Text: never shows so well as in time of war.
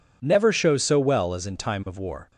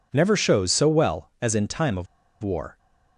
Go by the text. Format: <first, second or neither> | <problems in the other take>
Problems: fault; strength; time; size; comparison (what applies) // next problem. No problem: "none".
first | pauses between "of" and "war"; at 2.0 s; 0.37 s long